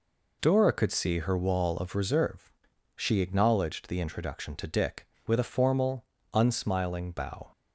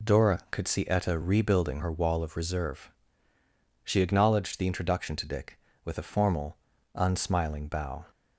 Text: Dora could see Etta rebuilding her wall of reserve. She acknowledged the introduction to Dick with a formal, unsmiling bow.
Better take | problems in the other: second | skips "Etta rebuilding"; at 1.1 s

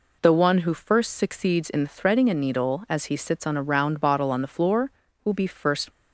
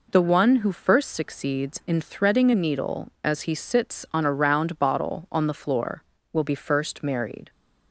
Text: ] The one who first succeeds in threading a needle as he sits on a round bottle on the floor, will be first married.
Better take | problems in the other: second | stops before "married"; at 5.9 s

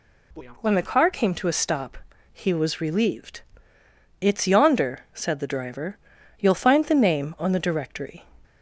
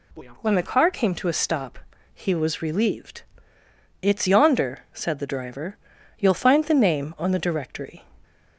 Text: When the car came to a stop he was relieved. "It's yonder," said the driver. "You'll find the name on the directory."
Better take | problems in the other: neither | pauses between "stop" and "he"; slight; the same in both

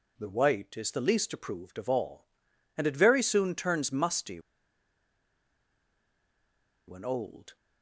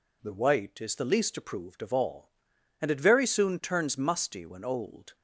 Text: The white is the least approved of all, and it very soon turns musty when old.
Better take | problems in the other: second | pauses between "musty" and "when"; strong; at 4.3 s; 2.4 s long

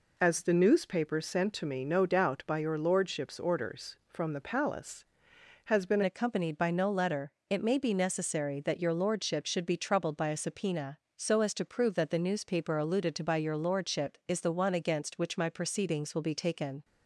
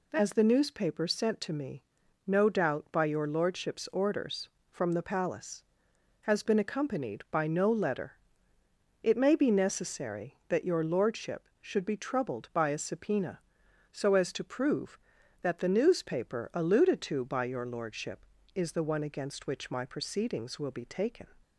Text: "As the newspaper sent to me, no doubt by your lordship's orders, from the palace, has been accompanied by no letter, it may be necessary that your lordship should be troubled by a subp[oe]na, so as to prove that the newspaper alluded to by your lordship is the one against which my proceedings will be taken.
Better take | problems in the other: second | changes voice at "accompanied"; from 6.0 s on; 10.8 s long

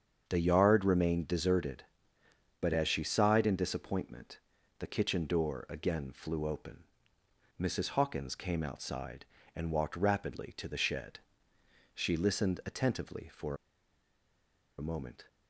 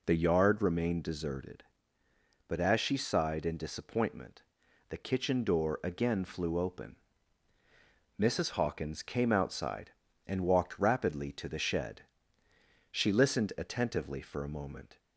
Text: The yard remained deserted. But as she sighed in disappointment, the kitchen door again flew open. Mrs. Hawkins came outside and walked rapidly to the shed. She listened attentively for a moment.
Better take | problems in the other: second | starts louder than the rest; strong; until 1.2 s; 7.5 dB // pauses between "for" and "a"; at 13.5 s; 1.2 s long

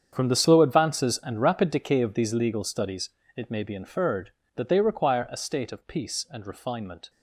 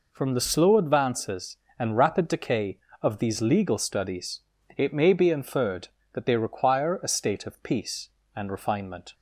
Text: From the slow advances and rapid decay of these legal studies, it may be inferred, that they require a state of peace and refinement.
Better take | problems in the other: second | gets quieter; strong; throughout; 15 dB

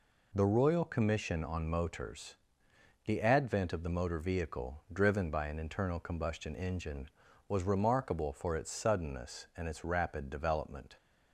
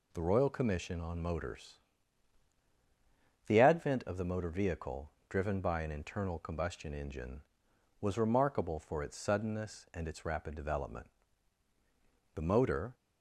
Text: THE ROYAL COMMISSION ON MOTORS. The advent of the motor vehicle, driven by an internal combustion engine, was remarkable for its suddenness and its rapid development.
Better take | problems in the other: first | goes on to say "The motor"; from 12.3 s on; 0.60 s long

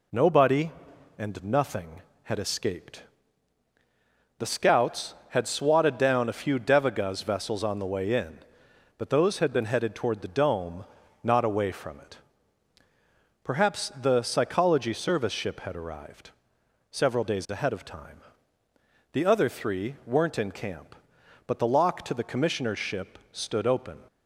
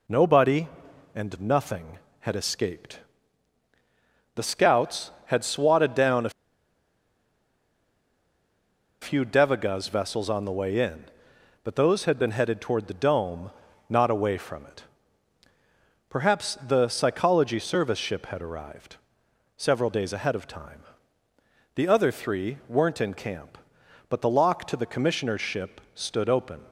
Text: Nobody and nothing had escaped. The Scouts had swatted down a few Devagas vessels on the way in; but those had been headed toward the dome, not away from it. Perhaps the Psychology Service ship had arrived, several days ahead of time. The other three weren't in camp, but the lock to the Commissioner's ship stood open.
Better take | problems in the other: first | pauses between "a" and "few"; strong; at 6.3 s; 2.7 s long

